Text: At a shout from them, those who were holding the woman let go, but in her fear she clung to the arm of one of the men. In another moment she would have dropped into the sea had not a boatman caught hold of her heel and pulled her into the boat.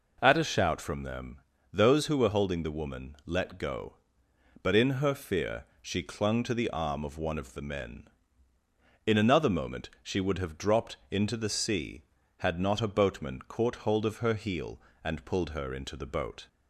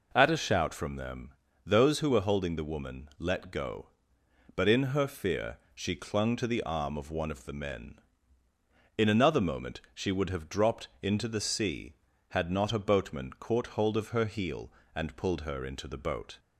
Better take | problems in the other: neither | pauses between "dropped" and "into"; slight; the same in both

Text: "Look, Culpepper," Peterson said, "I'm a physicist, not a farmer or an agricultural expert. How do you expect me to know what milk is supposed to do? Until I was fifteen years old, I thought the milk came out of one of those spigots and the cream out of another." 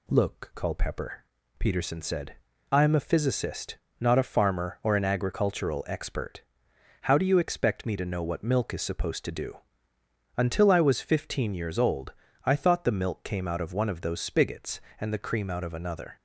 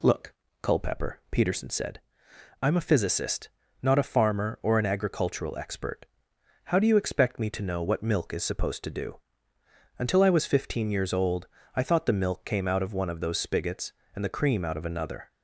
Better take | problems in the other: neither | none

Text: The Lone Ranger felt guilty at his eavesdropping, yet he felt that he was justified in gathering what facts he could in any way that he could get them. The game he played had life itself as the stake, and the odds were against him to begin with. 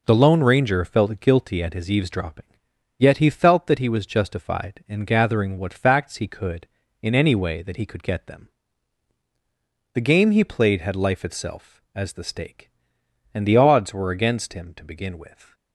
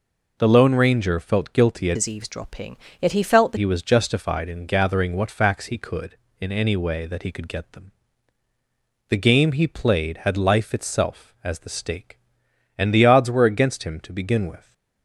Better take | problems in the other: first | changes voice from "his" to "that"; from 1.9 to 3.5 s; 1.6 s long

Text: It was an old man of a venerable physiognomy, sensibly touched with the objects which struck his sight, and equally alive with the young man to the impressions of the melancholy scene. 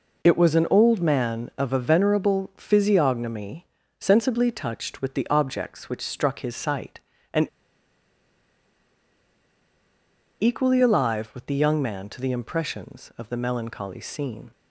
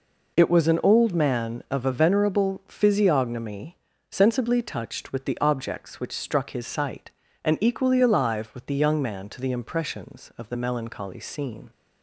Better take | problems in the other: second | pauses between "and" and "equally"; strong; at 7.4 s; 2.9 s long

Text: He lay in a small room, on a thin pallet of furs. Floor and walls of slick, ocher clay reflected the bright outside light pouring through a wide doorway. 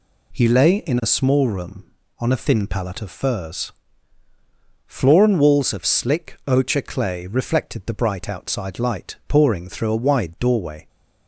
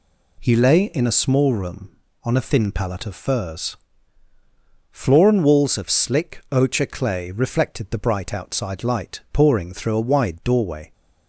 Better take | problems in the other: neither | none

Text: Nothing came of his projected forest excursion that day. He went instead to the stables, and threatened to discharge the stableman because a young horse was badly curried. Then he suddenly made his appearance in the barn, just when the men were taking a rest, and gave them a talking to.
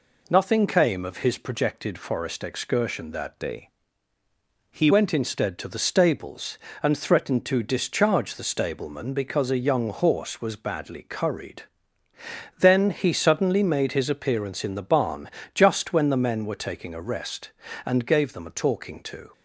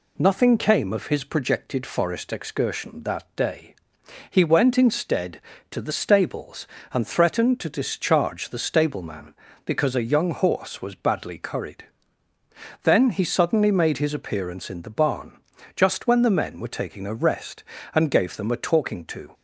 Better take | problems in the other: second | changes voice from "day" to "He"; from 3.3 to 4.8 s; 1.5 s long

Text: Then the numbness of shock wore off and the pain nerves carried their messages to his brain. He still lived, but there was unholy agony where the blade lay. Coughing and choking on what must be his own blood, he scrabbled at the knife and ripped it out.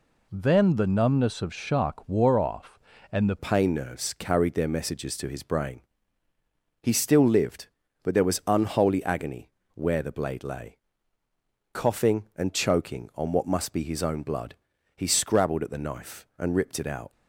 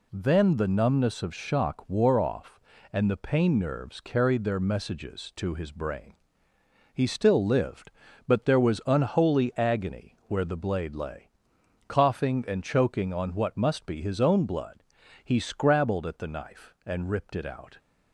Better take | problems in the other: second | changes voice at "pain"; from 3.3 s on; 13.8 s long // pauses between "agony" and "where"; slight; at 9.4 s; 0.24 s long

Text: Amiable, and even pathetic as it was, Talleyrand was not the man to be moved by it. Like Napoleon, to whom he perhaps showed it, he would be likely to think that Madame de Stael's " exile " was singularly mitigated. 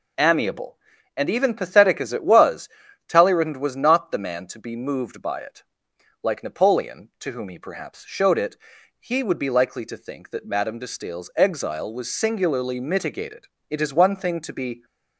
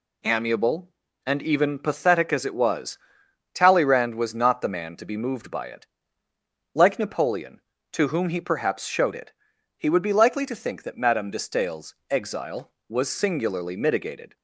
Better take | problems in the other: second | goes on to say "It is one thing to be"; noticeable; from 13.6 s on; 1.1 s long

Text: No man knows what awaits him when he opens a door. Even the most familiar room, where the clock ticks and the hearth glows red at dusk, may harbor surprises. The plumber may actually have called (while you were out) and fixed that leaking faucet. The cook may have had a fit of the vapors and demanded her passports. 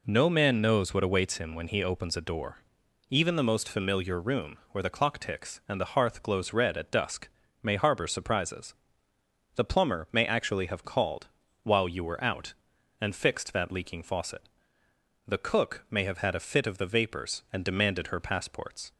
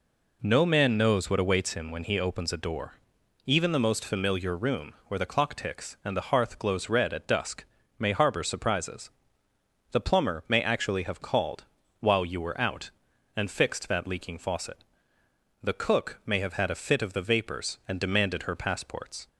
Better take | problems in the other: neither | none

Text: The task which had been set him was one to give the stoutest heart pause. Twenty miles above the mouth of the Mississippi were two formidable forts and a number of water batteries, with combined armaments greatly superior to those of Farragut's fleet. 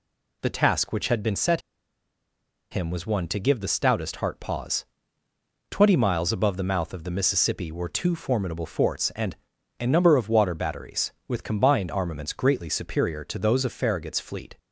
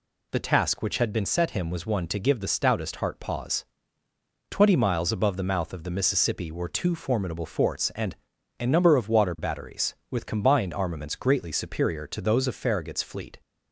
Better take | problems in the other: second | pauses between "set" and "him"; at 1.6 s; 1.1 s long // pauses between "and" and "a"; at 9.3 s; 0.44 s long; also in the second

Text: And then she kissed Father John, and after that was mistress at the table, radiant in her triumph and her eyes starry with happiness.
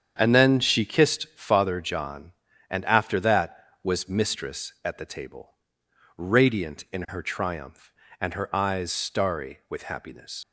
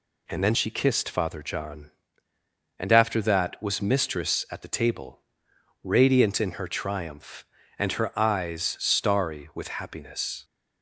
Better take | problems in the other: second | starts louder than the rest; strong; until 1.1 s; 8 dB // leaves "happiness" unfinished; at 10.4 s; 90 ms

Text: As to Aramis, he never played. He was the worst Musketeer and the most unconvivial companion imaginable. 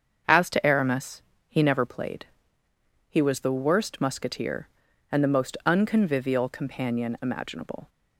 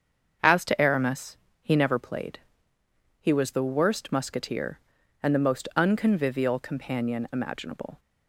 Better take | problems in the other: neither | starts louder than the rest; the same in both

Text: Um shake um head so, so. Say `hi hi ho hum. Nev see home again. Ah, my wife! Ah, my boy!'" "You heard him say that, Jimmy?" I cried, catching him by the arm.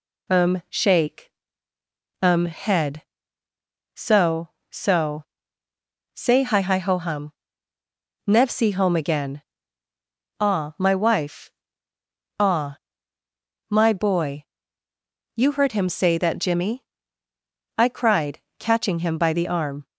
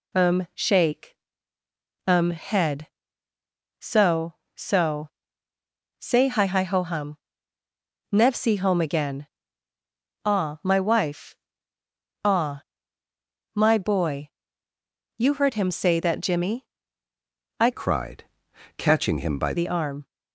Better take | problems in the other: first | pauses between "shake" and "um"; noticeable; at 1.1 s; 0.90 s long; noticeable in the first // changes voice from "cried" to "by"; from 17.7 to 19.5 s; 1.8 s long

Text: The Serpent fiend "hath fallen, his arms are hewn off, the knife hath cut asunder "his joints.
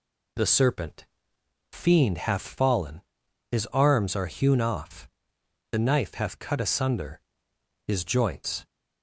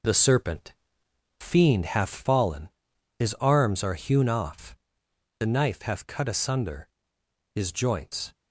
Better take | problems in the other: first | gets quieter; noticeable; throughout; 6 dB // pauses between "Serpent" and "fiend"; noticeable; at 0.7 s; 0.66 s long; noticeable in the first // pauses between "asunder" and "his"; noticeable; at 6.8 s; 0.66 s long; noticeable in the first

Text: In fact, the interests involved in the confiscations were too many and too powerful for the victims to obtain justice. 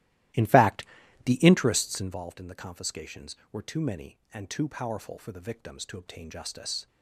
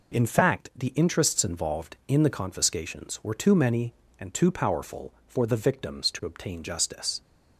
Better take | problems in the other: second | starts louder than the rest; strong; until 2.2 s; 15 dB

